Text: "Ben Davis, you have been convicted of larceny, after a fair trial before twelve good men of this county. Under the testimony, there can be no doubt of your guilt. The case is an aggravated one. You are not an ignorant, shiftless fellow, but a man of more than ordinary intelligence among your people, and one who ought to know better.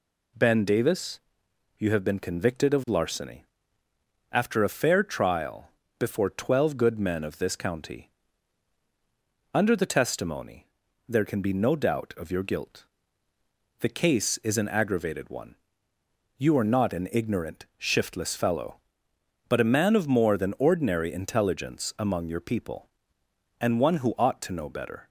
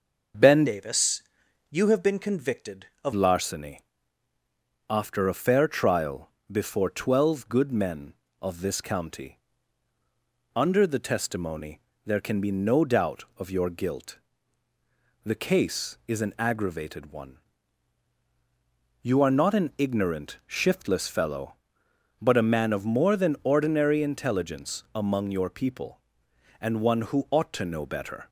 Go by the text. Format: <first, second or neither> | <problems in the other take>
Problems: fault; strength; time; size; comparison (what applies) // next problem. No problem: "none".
first | changes voice from "Davis" to "of"; from 0.6 to 3.1 s; 2.5 s long // pauses between "trial" and "before"; slight; at 6.2 s; 0.22 s long; slight in the first